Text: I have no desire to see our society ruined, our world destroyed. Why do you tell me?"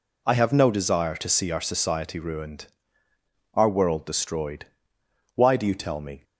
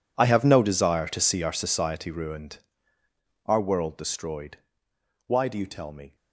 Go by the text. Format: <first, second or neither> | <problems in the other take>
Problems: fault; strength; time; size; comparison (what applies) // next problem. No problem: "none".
first | gets quieter; strong; throughout; 18 dB